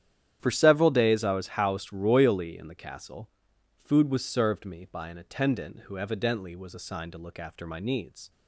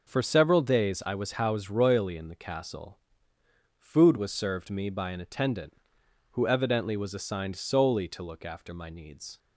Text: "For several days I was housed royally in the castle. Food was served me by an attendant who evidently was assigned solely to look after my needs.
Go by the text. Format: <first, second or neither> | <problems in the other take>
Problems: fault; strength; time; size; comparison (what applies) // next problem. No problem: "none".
second | starts louder than the rest; strong; until 1.4 s; 10 dB // skips "solely"; at 7.1 s